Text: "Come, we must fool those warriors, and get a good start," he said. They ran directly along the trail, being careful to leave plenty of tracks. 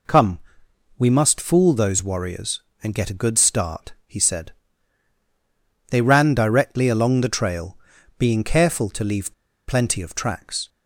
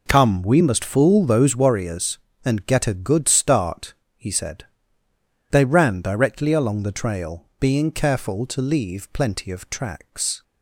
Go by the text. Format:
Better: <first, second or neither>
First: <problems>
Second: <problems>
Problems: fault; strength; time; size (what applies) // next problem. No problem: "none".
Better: second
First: pauses between "leave" and "plenty"; slight; at 9.3 s; 0.34 s long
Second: none